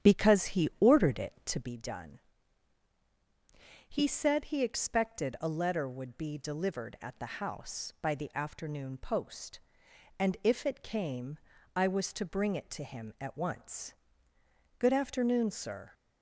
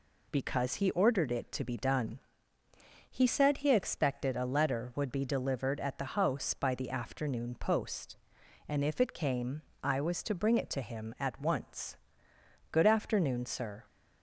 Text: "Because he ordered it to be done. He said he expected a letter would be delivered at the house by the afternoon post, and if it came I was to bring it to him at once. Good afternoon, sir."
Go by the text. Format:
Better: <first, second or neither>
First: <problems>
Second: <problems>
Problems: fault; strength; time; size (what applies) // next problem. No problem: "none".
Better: second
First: starts louder than the rest; strong; until 1.7 s; 9 dB // pauses between "came" and "I"; slight; at 11.3 s; 0.36 s long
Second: pauses between "came" and "I"; slight; at 9.6 s; 0.20 s long